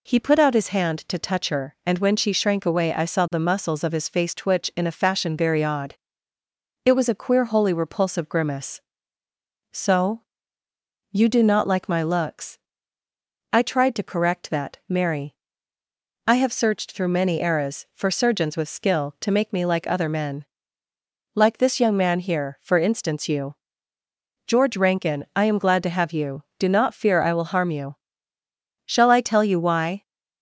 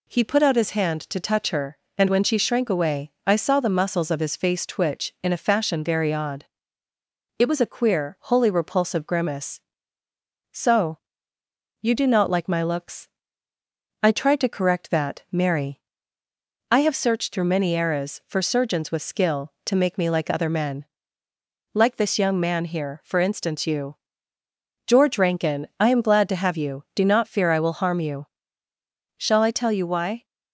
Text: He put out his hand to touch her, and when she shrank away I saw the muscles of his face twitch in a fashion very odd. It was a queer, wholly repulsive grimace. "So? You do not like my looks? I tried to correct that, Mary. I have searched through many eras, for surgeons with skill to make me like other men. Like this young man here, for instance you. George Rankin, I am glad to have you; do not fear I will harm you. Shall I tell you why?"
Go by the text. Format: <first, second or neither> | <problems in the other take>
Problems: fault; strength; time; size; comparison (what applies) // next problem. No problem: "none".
neither | none